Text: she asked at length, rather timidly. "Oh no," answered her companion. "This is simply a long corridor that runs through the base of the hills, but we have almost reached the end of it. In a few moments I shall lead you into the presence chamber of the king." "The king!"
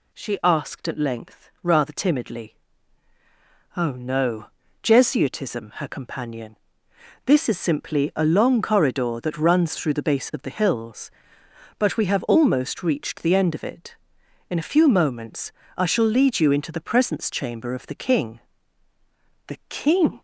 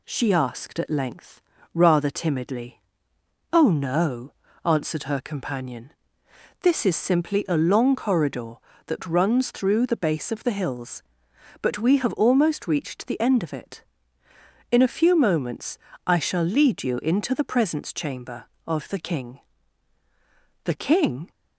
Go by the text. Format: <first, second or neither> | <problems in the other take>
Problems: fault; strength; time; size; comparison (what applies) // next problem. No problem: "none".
second | says "jesuitism" for "answered"; at 4.8 s // pauses between "moments" and "I"; slight; at 15.5 s; 0.24 s long; slight in the second